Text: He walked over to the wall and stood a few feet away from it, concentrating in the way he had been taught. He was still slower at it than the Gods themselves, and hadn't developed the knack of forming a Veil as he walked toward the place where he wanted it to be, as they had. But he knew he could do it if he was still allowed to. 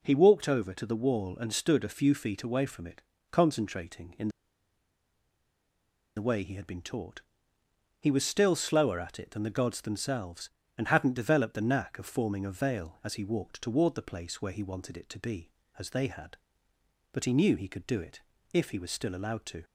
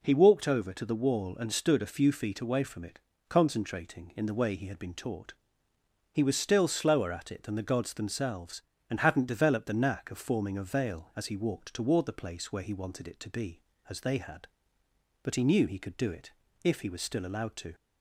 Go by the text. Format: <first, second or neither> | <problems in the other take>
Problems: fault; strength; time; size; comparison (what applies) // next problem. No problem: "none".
second | pauses between "in" and "the"; strong; at 4.2 s; 1.8 s long // pauses between "it" and "if"; slight; at 18.1 s; 0.32 s long; slight in the second